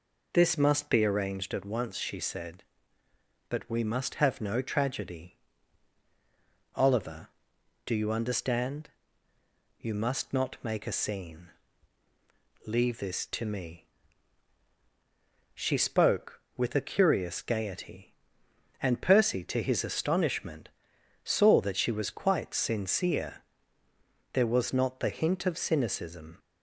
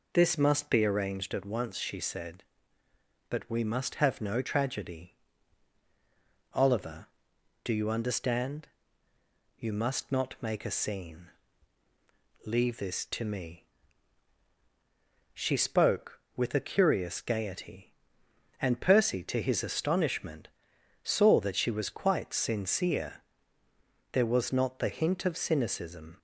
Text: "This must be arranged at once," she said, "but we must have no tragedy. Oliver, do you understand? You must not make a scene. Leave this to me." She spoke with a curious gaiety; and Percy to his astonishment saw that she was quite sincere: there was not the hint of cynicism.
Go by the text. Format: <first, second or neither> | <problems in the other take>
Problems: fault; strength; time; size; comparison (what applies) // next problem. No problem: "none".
neither | pauses between "astonishment" and "saw"; noticeable; the same in both